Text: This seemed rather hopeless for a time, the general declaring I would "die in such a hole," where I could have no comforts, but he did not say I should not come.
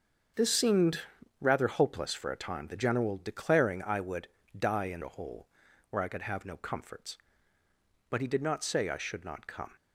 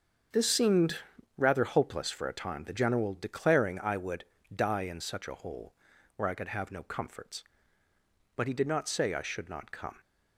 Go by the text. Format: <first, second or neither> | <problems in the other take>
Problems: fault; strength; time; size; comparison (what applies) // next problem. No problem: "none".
second | starts louder than the rest; until 1.7 s; 7 dB; also in the second // pauses between "seemed" and "rather"; at 1.0 s; 0.40 s long; also in the second // pauses between "would" and "die"; slight; at 4.2 s; 0.30 s long; slight in the second // skips "such"; at 5.0 s